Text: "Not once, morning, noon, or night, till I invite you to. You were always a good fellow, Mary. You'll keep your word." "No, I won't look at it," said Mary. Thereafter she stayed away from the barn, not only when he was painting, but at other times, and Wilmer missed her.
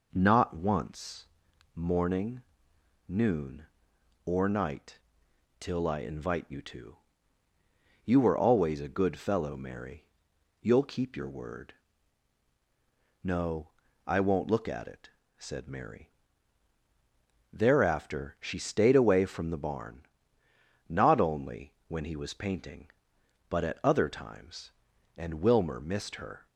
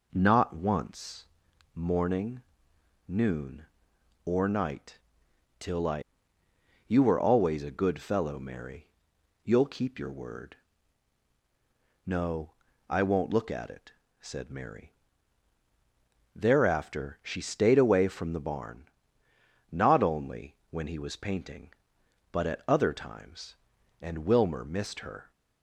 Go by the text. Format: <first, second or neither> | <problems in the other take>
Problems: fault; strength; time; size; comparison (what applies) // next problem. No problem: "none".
first | skips "invite you to"; at 6.4 s